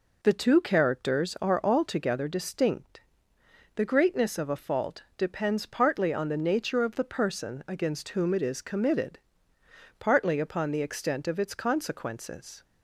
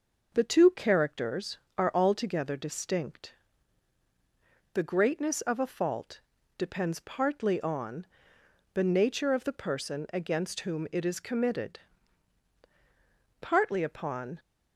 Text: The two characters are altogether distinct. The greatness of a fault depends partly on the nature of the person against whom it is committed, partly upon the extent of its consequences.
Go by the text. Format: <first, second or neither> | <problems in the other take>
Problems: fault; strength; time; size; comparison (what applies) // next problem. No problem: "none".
first | pauses between "fault" and "depends"; slight; at 6.2 s; 0.36 s long // pauses between "on" and "the"; noticeable; at 8.0 s; 0.66 s long // stops before "the extent of its consequences"; at 14.3 s